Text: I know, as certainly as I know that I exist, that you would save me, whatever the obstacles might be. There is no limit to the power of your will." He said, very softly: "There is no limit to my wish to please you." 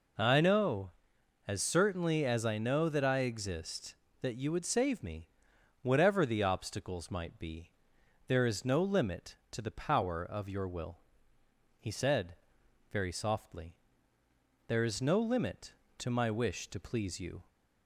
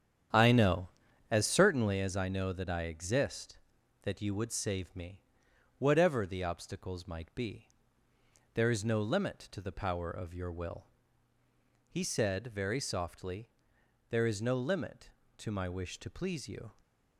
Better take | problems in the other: first | starts louder than the rest; strong; until 2.0 s; 9 dB

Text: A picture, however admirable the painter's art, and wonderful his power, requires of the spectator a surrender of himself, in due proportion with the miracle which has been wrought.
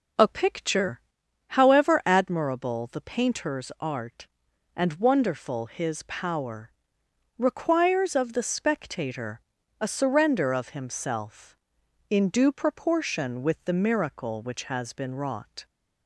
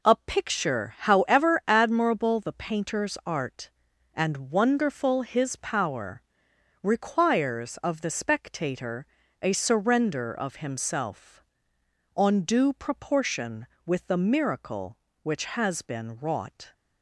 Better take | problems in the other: first | pauses between "spectator" and "a"; at 9.0 s; 0.38 s long; also in the first // says "on" for "in"; at 12.1 s

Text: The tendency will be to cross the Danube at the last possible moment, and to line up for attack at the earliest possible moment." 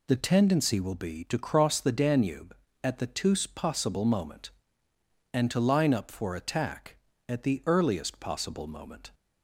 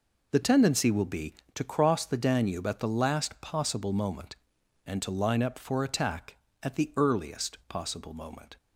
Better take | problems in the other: second | says "tous" for "last"; at 3.0 s

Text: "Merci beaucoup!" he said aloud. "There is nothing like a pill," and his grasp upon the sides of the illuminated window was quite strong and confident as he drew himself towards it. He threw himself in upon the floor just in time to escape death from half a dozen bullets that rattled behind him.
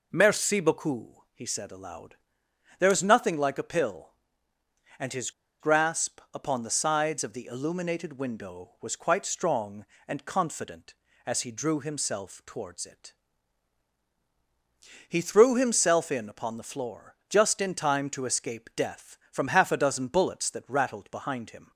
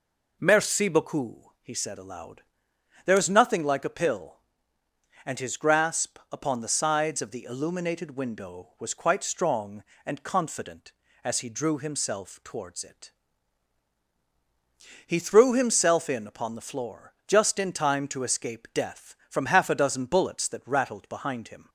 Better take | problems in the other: second | pauses between "his" and "grasp"; slight; at 5.3 s; 0.29 s long

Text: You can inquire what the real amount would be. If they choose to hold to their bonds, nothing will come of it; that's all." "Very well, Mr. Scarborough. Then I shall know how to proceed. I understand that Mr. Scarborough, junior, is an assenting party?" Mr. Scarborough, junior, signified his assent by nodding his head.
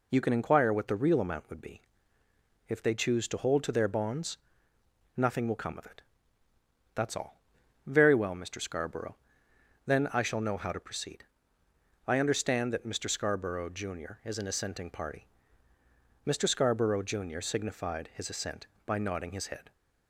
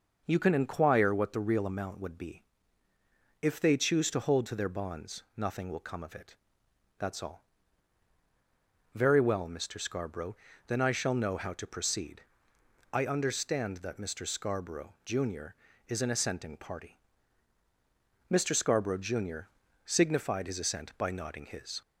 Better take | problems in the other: first | stops before "head"; at 21.8 s

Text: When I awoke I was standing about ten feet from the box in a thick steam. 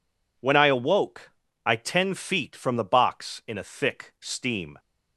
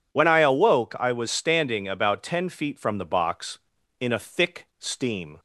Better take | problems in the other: second | pauses between "awoke" and "I"; slight; at 1.3 s; 0.34 s long // skips "was standing about"; at 1.7 s

